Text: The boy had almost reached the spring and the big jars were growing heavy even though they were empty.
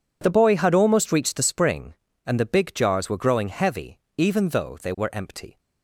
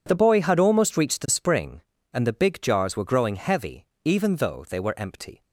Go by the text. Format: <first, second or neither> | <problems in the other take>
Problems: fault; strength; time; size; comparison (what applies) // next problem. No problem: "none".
neither | pauses between "heavy" and "even"; slight; the same in both